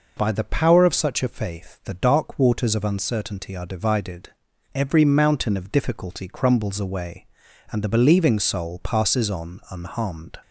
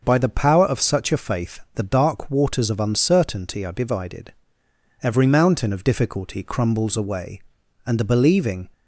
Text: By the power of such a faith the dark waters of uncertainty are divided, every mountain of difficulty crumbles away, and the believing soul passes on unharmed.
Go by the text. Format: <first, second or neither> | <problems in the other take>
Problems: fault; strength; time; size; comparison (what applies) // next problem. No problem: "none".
first | starts louder than the rest; until 1.0 s; 6.5 dB // pauses between "faith" and "the"; slight; at 1.5 s; 0.16 s long // stops before "soul passes on unharmed"; at 8.7 s